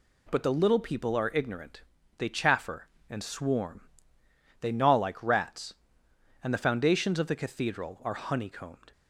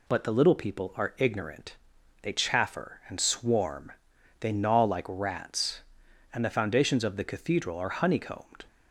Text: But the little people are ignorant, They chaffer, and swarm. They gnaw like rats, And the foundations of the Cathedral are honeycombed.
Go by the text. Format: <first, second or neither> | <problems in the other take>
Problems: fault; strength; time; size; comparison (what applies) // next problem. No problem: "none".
neither | none